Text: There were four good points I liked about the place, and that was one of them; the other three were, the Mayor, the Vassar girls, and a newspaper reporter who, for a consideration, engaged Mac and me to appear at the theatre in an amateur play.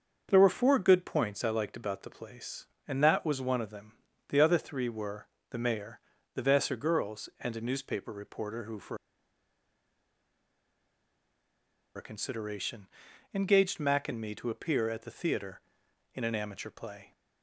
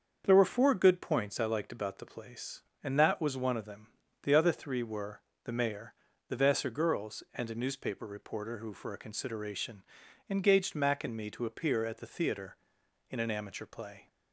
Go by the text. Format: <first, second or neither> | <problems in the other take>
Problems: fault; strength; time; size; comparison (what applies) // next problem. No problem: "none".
second | starts louder than the rest; until 1.3 s; 6.5 dB; also in the second // pauses between "for" and "a"; strong; at 8.9 s; 3.0 s long